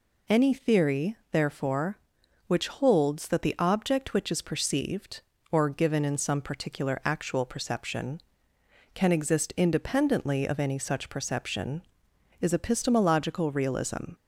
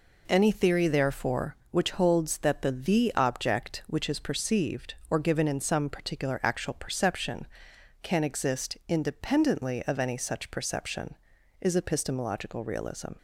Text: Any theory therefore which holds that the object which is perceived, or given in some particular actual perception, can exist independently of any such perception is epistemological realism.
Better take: first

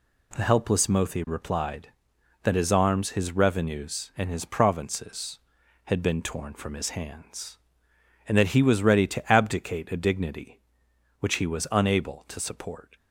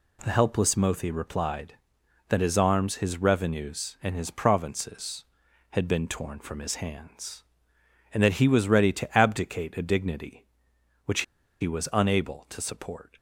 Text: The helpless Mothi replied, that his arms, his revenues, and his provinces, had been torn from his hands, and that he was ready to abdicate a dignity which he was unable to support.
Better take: first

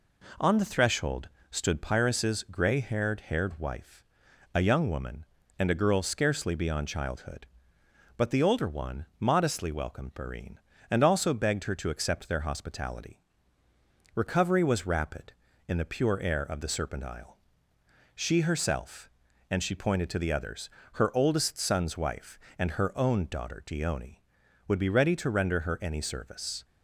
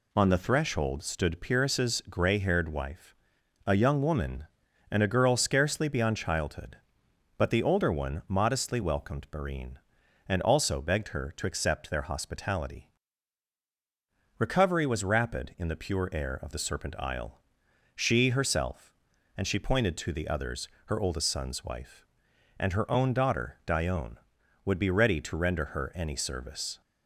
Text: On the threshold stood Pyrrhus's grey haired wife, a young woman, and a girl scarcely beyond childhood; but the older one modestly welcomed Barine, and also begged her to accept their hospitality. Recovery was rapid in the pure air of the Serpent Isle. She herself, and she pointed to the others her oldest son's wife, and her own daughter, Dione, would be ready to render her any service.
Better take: second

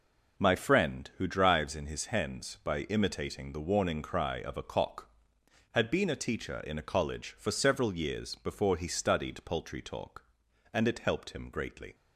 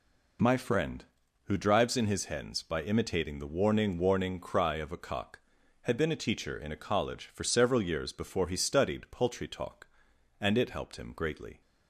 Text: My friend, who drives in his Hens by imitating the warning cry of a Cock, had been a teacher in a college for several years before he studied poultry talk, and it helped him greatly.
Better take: first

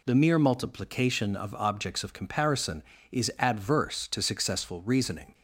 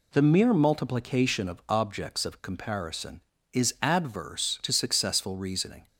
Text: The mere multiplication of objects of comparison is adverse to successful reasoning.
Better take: neither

